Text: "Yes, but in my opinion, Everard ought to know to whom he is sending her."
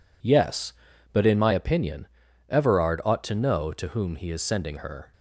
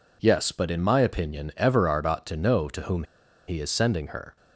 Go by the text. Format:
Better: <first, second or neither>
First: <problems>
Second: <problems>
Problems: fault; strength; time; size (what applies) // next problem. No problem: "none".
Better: first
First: none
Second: pauses between "whom" and "he"; at 3.0 s; 0.44 s long